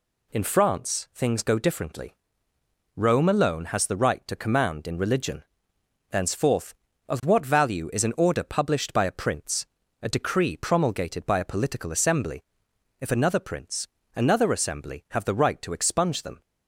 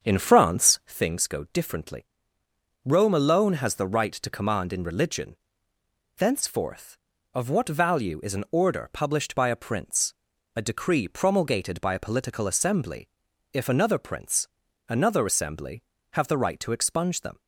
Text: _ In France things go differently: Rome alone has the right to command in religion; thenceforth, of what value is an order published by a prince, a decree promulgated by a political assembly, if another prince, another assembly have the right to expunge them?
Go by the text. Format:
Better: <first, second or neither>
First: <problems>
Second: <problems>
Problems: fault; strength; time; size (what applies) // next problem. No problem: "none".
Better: first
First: none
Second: starts louder than the rest; strong; until 1.0 s; 7 dB